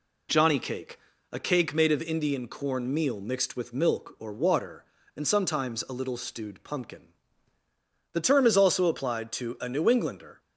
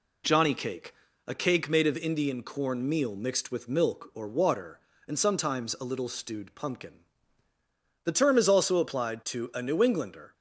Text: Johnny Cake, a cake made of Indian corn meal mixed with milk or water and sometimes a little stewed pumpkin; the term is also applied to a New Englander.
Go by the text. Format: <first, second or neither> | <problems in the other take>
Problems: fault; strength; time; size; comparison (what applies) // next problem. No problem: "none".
neither | none